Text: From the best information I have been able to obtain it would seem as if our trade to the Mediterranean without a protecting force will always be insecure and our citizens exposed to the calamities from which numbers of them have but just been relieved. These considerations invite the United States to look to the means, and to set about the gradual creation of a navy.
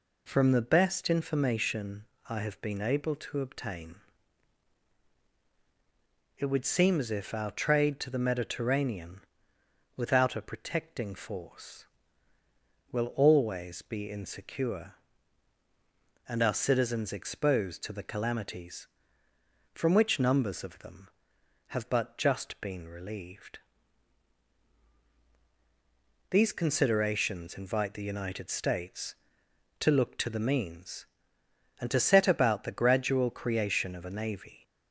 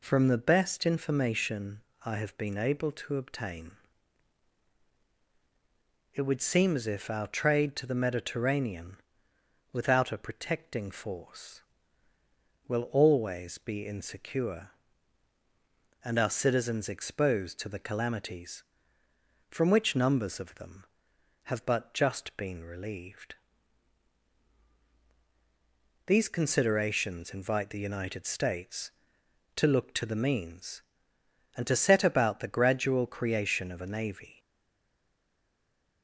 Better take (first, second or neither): first